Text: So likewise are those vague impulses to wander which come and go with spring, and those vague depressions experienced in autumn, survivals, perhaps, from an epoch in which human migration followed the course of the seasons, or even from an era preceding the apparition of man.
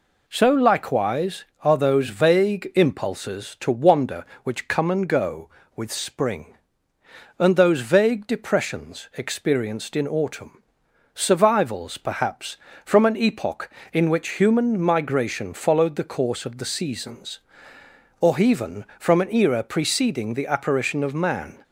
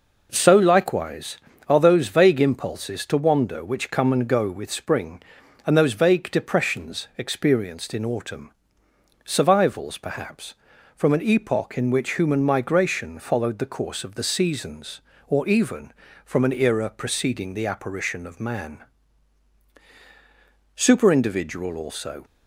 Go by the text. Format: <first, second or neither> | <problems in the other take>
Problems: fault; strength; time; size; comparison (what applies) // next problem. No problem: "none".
first | goes on to say "Superindividual also"; from 20.7 s on; 1.4 s long